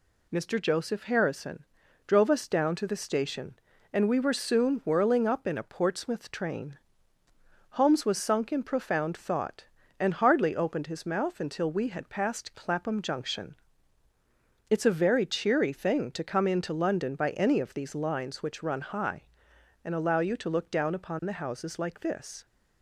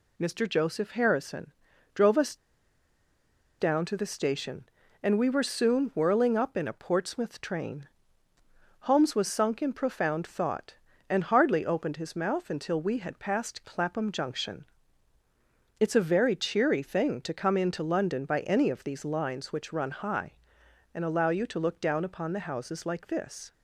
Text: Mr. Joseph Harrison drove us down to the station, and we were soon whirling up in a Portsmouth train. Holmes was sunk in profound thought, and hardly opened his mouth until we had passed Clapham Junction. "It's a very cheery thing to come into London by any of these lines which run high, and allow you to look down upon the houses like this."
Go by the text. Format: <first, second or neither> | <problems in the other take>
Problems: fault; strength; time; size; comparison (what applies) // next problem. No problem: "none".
first | pauses between "Harrison" and "drove"; at 1.5 s; 0.42 s long; also in the first // pauses between "us" and "down"; at 2.3 s; 1.2 s long